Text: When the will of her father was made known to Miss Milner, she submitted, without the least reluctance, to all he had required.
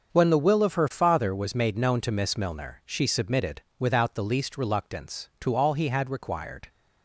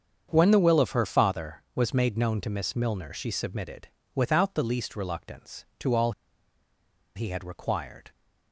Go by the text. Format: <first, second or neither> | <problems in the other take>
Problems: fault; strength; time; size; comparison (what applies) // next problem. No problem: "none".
first | starts louder than the rest; strong; until 1.3 s; 7 dB; also in the first // pauses between "all" and "he"; at 6.1 s; 1.0 s long